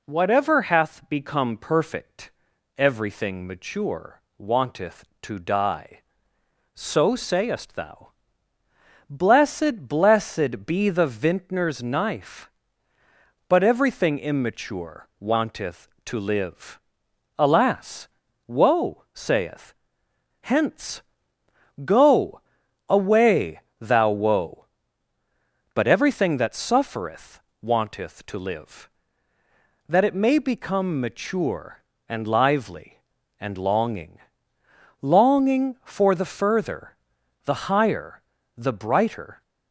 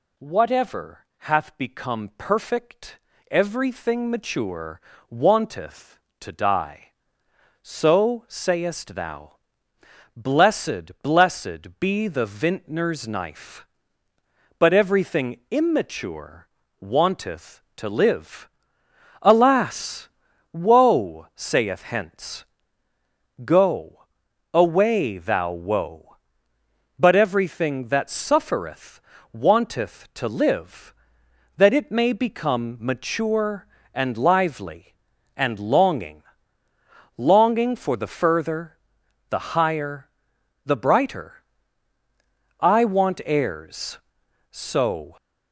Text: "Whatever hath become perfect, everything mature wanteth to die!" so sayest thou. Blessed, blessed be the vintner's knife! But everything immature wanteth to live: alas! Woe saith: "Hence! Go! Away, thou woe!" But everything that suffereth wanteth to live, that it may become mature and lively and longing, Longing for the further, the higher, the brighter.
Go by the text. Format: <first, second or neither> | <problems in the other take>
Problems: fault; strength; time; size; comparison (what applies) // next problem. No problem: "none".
first | pauses between "mature" and "wanteth"; slight; at 4.7 s; 0.30 s long; slight in the first // pauses between "immature" and "wanteth"; slight; at 16.4 s; 0.34 s long // pauses between "suffereth" and "wanteth"; slight; at 28.9 s; 0.32 s long; slight in the first // goes on to say "I want heirs so"; strong; from 42.5 s on; 2.5 s long